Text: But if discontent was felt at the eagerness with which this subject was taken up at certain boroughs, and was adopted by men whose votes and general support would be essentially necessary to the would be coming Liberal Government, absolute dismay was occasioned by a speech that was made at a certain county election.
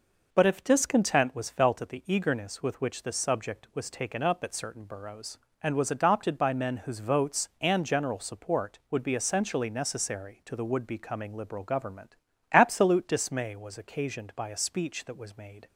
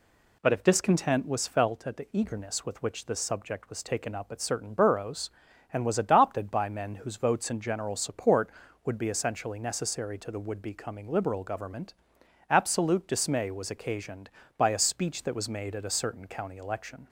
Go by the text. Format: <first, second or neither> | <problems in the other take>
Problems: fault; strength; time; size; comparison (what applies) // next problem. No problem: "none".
second | stops before "at a certain county election"; at 15.6 s